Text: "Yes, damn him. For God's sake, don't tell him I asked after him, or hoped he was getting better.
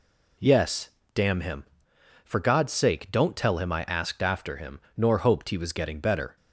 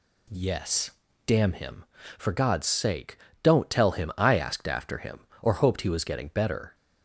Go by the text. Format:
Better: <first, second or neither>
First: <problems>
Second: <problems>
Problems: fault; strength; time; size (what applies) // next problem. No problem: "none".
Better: second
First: says "nor" for "or"; at 4.9 s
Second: none